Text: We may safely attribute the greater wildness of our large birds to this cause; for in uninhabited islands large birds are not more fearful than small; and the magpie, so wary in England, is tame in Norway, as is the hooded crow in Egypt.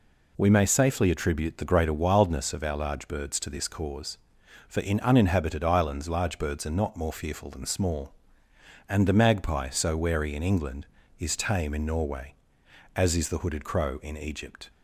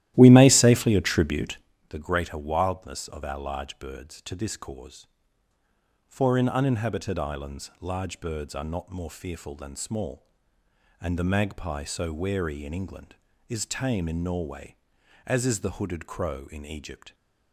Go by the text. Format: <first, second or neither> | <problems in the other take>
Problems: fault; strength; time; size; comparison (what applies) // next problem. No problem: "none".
first | starts louder than the rest; strong; until 1.7 s; 14 dB // pauses between "attribute" and "the"; slight; at 1.5 s; 0.30 s long